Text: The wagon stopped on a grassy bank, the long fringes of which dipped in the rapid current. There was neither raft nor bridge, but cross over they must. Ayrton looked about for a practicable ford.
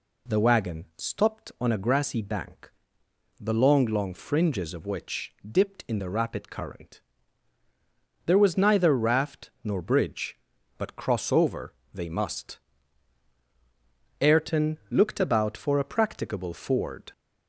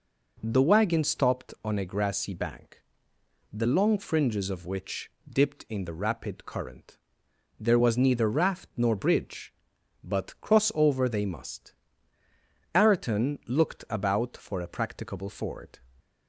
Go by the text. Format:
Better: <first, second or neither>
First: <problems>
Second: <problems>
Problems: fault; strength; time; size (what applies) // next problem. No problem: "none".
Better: second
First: says "long" twice; at 3.8 s // pauses between "which" and "dipped"; slight; at 5.3 s; 0.16 s long // pauses between "over" and "they"; slight; at 11.7 s; 0.20 s long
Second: pauses between "which" and "dipped"; slight; at 5.0 s; 0.18 s long